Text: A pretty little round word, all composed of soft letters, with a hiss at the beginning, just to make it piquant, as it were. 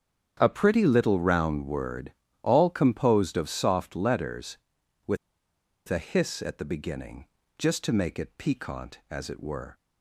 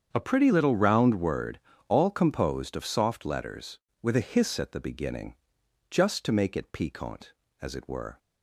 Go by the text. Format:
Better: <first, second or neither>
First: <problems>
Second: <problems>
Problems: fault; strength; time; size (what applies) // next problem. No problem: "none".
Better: second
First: starts louder than the rest; strong; until 1.4 s; 8.5 dB // pauses between "with" and "a"; noticeable; at 5.1 s; 0.71 s long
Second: starts louder than the rest; strong; until 1.1 s; 7.5 dB